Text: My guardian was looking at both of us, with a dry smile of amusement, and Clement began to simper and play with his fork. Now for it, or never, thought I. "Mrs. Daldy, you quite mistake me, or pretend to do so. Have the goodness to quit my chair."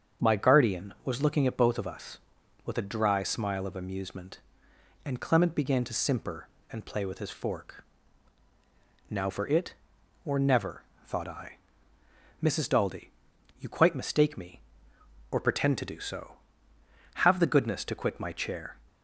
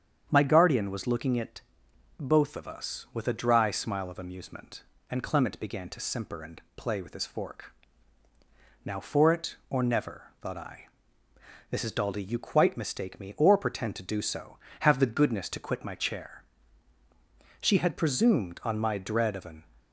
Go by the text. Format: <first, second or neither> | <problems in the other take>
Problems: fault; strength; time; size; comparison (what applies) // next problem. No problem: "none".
first | starts louder than the rest; strong; until 1.3 s; 8 dB; strong in the first // pauses between "at" and "both"; noticeable; at 1.6 s; 0.58 s long // goes on to say "She had presumed on my dread of an"; strong; from 17.5 s on; 2.0 s long